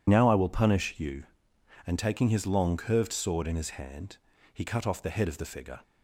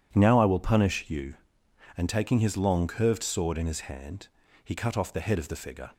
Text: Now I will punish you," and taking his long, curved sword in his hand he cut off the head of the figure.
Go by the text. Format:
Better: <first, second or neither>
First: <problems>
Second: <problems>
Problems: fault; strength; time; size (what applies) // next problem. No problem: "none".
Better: second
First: loses the start of "Now"; at 0.0 s; 75 ms // pauses between "hand" and "he"; slight; at 4.1 s; 0.34 s long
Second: pauses between "hand" and "he"; slight; at 4.2 s; 0.34 s long